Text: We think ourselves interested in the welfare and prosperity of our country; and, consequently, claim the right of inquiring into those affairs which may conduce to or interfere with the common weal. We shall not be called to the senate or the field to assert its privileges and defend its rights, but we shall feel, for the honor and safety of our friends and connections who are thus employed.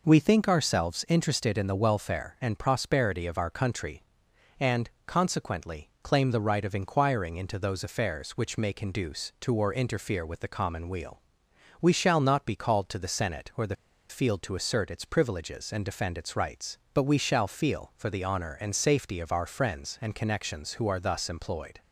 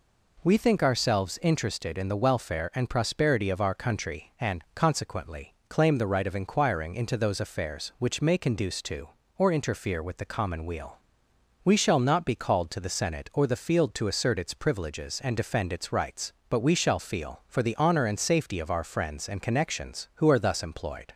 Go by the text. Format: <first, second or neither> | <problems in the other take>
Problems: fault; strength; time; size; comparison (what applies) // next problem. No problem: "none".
second | pauses between "the" and "field"; slight; at 13.7 s; 0.34 s long